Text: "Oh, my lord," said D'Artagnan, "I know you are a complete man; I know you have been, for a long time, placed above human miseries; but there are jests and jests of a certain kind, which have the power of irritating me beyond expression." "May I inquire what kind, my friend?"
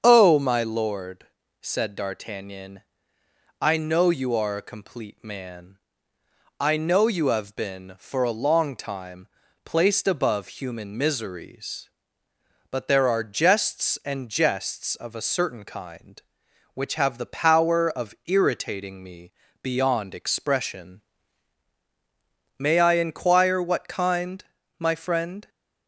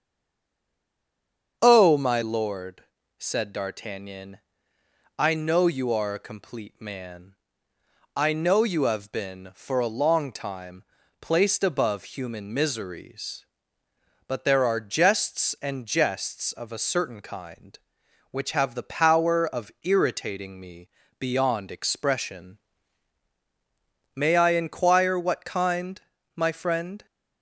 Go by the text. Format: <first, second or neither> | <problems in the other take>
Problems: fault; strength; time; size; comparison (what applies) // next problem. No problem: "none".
first | stays silent before the first word; noticeable; until 1.6 s; 1.6 s long // starts louder than the rest; strong; until 2.6 s; 7 dB; strong in the first // pauses between "me" and "beyond"; slight; at 20.8 s; 0.30 s long; slight in the first